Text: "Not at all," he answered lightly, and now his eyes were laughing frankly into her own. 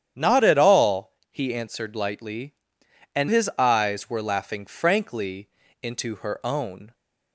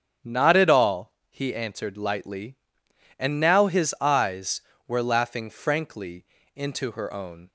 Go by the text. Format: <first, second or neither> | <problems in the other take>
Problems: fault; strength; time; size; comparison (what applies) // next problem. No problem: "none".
second | starts louder than the rest; strong; until 1.3 s; 9.5 dB; strong in the second // skips "now"; at 3.2 s // pauses between "frankly" and "into"; slight; at 5.4 s; 0.34 s long; slight in the second